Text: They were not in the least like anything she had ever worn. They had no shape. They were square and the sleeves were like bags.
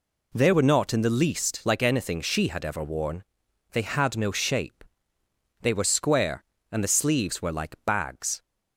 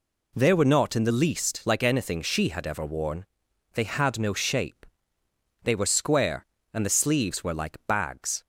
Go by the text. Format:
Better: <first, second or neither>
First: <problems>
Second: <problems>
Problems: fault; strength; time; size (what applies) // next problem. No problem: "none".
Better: neither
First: none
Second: none